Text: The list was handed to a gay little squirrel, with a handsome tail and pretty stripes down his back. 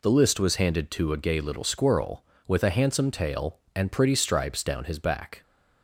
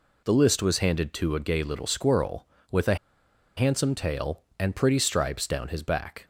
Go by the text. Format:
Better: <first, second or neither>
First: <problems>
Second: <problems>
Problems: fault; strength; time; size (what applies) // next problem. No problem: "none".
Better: first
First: none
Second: pauses between "a" and "handsome"; noticeable; at 2.9 s; 0.62 s long